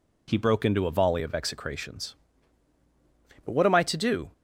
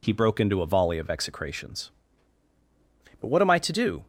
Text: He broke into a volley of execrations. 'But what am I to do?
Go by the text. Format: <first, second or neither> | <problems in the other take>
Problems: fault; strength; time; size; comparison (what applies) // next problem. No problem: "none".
neither | none